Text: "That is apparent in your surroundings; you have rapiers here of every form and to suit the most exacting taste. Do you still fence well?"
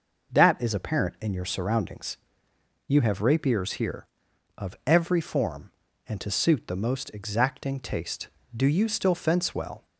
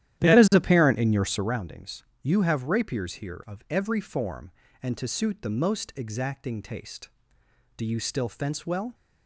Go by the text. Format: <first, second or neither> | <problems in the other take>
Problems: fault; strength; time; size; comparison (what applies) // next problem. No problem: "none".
first | starts louder than the rest; strong; until 1.6 s; 12 dB